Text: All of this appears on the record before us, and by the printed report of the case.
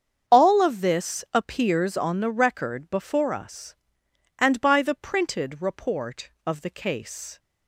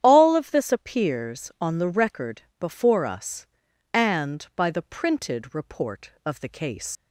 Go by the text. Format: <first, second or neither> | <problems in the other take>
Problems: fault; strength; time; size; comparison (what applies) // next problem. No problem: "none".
first | starts louder than the rest; strong; until 1.0 s; 10 dB; strong in the first // pauses between "record" and "before"; slight; at 2.4 s; 0.18 s long // leaves "case" unfinished; at 6.9 s; 95 ms